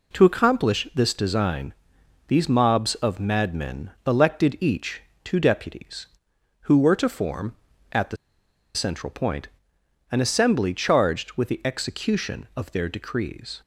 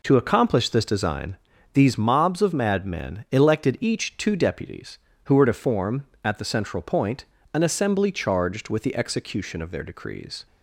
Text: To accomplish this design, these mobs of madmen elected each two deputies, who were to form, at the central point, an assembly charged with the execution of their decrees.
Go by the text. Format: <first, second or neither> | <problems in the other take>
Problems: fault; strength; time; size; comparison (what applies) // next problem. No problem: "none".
second | pauses between "each" and "two"; slight; at 5.0 s; 0.22 s long // pauses between "the" and "central"; noticeable; at 8.1 s; 0.58 s long